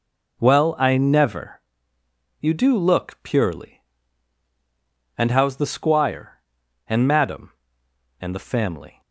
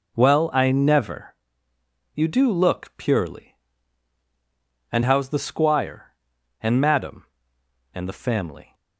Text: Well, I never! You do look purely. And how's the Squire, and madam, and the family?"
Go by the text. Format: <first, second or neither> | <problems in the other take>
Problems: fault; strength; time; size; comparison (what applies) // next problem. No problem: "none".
neither | none